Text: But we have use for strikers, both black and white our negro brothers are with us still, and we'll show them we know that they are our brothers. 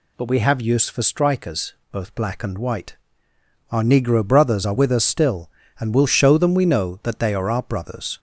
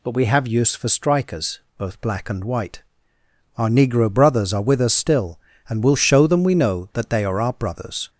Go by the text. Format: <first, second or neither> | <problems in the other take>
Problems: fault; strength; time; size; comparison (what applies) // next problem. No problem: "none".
neither | pauses between "white" and "our"; noticeable; the same in both